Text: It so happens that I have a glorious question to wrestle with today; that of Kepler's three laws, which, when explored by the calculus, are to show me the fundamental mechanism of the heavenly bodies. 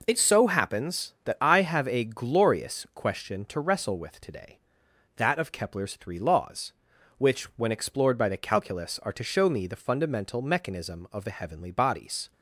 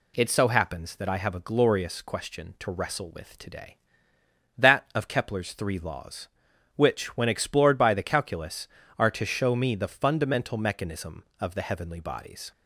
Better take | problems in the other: neither | none

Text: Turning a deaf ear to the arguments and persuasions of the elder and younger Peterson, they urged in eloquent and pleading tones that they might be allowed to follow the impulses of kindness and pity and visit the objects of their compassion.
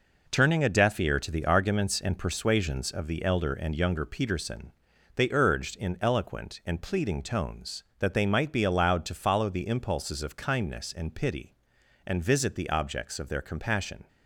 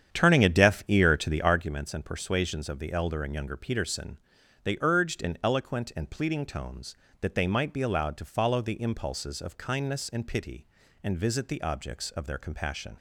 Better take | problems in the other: first | starts louder than the rest; strong; until 1.7 s; 9 dB

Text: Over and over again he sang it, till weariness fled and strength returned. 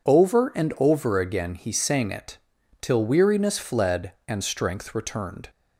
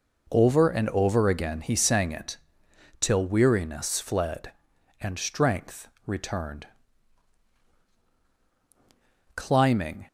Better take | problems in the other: first | pauses between "strength" and "returned"; slight; at 5.8 s; 0.18 s long // goes on to say "Climbing"; noticeable; from 9.3 s on; 0.72 s long

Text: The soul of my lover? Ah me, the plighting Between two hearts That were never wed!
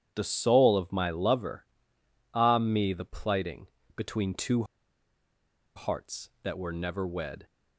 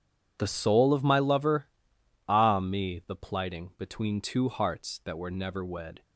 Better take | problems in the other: second | starts louder than the rest; strong; until 1.1 s; 9.5 dB // pauses between "plighting" and "Between"; slight; at 3.6 s; 0.28 s long // pauses between "two" and "hearts"; at 4.6 s; 1.1 s long

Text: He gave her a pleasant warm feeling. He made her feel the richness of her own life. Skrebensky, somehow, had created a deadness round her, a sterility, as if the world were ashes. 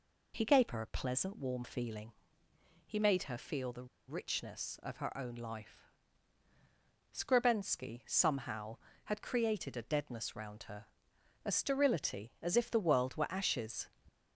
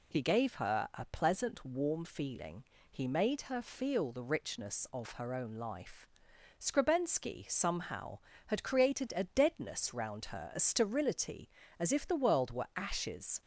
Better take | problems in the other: second | pauses between "the" and "richness"; slight; at 3.8 s; 0.20 s long

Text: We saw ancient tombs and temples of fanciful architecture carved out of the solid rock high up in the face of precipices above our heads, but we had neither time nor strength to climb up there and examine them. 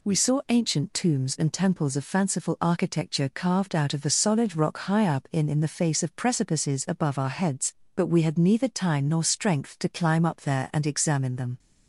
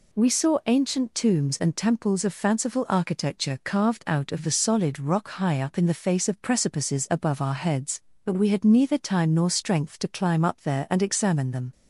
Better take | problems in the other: second | says "in" twice; at 5.4 s

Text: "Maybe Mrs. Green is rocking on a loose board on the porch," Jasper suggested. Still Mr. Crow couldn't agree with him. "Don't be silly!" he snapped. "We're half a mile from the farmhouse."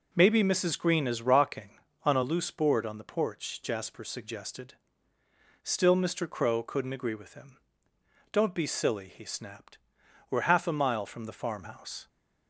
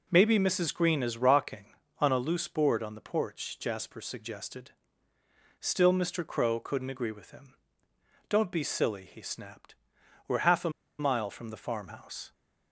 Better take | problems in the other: first | pauses between "a" and "mile"; slight; at 10.6 s; 0.29 s long

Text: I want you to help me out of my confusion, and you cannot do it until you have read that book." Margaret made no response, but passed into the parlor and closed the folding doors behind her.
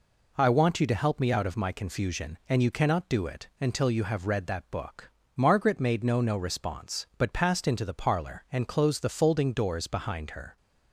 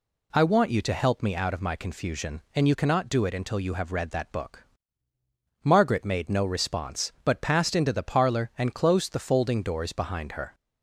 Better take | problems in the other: second | says "no" twice; at 6.2 s

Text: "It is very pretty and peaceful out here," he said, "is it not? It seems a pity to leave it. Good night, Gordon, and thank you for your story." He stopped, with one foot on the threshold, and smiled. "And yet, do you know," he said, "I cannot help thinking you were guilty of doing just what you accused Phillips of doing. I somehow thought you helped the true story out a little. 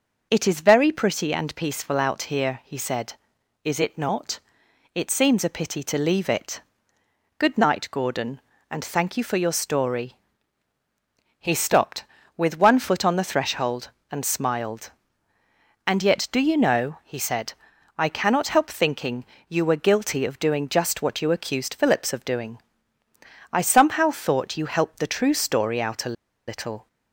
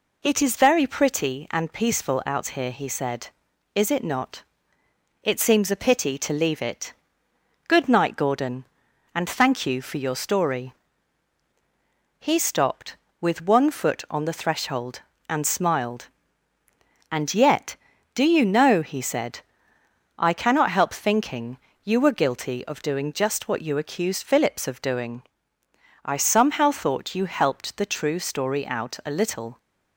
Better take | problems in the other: second | pauses between "thinking" and "you"; slight; at 19.2 s; 0.22 s long; slight in the second // pauses between "a" and "little"; slight; at 26.1 s; 0.32 s long

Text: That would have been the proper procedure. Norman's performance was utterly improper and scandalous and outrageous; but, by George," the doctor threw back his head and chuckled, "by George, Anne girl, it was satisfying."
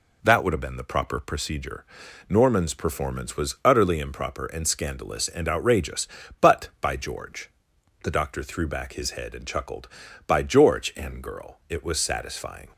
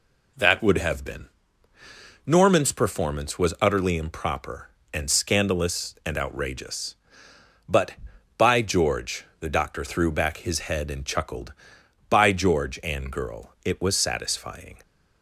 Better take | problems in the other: first | skips "the proper procedure"; at 1.7 s

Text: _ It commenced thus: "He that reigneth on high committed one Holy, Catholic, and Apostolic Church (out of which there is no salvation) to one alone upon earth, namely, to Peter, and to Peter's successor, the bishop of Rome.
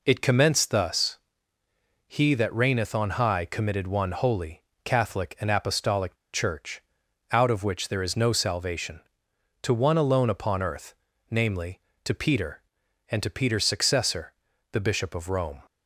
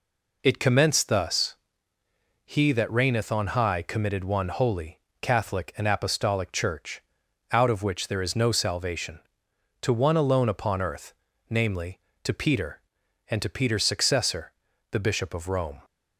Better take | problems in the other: second | pauses between "Apostolic" and "Church"; slight; at 6.1 s; 0.17 s long

